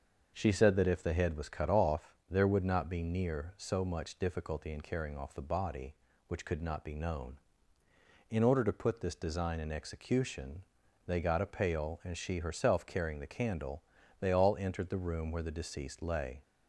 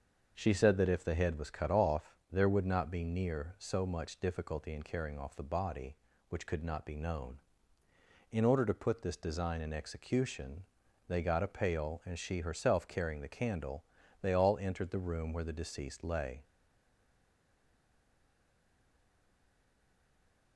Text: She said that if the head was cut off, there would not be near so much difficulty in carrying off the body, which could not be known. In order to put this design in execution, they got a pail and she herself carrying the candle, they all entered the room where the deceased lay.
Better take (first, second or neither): first